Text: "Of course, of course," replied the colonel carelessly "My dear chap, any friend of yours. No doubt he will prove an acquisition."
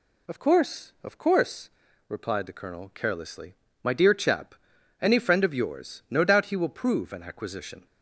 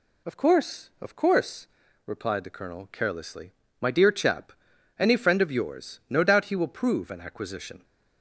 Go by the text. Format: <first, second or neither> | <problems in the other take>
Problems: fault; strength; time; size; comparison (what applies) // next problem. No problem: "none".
neither | pauses between "carelessly" and "My"; slight; the same in both